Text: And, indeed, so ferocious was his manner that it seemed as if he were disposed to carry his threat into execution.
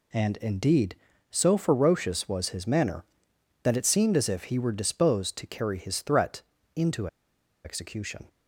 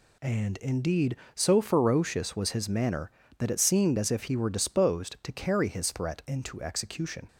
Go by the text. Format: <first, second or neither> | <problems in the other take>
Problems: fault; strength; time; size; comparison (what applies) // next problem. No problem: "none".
second | pauses between "threat" and "into"; slight; at 6.4 s; 0.34 s long // pauses between "into" and "execution"; noticeable; at 7.0 s; 0.57 s long